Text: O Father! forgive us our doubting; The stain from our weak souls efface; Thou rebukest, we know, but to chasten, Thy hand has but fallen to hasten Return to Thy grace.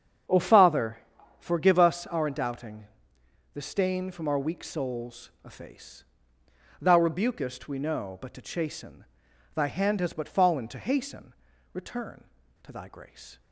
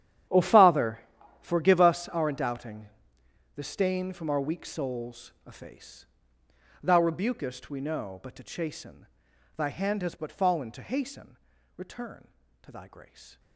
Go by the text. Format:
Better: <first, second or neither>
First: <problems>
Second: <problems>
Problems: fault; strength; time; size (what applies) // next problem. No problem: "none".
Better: first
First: starts louder than the rest; strong; until 1.6 s; 7.5 dB // pauses between "hasten" and "Return"; at 11.3 s; 0.40 s long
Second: gets quieter; strong; throughout; 16.5 dB // starts louder than the rest; strong; until 1.7 s; 10.5 dB // pauses between "hasten" and "Return"; at 11.3 s; 0.40 s long